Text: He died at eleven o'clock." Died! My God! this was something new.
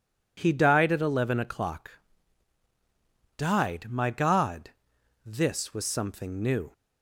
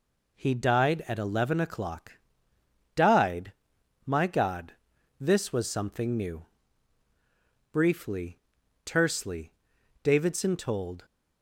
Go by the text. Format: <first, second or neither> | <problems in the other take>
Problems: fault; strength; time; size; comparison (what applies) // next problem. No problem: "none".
first | goes on to say "Briefly tersely Davidson told"; strong; from 7.7 s on; 3.3 s long